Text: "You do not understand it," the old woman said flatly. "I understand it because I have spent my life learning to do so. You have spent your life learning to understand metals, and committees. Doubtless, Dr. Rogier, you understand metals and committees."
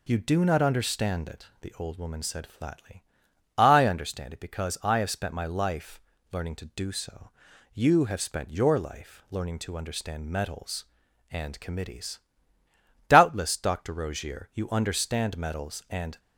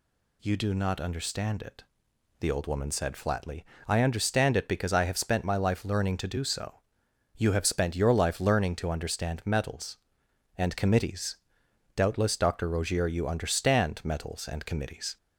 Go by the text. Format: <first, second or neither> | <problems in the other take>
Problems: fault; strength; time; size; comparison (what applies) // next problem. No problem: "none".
second | pauses between "life" and "learning"; slight; at 5.9 s; 0.30 s long // stops before "committees"; at 16.1 s